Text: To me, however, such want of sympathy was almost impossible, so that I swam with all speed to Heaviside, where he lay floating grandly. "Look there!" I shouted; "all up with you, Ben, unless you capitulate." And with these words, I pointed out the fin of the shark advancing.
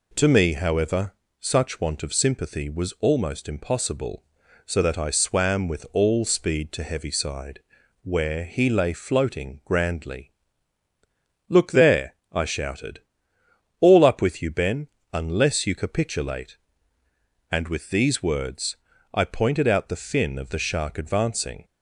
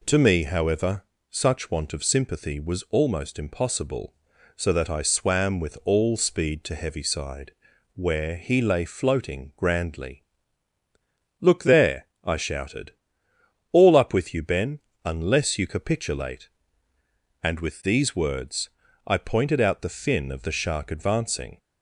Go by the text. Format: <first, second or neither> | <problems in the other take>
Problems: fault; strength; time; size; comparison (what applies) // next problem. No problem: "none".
neither | none